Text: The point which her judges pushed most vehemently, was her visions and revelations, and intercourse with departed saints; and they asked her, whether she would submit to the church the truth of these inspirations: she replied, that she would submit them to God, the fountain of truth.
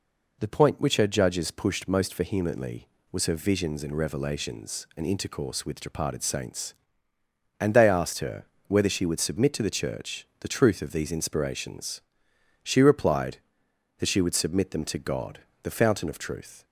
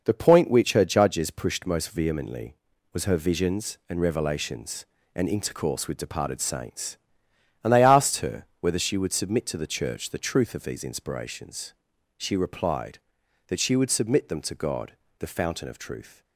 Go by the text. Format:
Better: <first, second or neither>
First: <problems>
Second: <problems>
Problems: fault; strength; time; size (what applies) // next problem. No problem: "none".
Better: neither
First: none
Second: none